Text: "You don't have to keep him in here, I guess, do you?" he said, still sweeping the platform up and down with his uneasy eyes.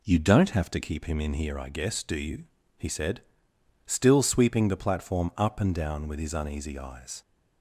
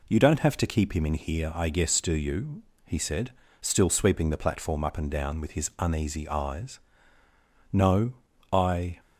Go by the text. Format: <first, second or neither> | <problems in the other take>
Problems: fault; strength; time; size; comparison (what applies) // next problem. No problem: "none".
first | goes on to say "No I"; noticeable; from 7.7 s on; 1.2 s long